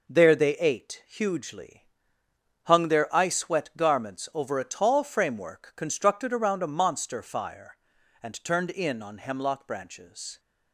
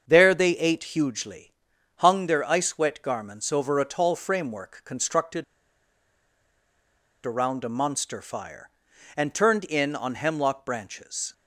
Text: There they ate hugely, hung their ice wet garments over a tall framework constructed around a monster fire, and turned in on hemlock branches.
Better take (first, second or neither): first